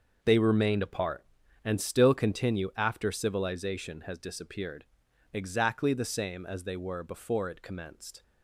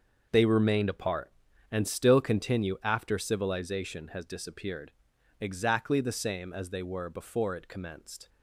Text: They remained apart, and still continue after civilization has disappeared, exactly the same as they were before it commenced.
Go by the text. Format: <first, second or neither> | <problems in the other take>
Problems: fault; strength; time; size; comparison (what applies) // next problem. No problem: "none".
neither | starts louder than the rest; the same in both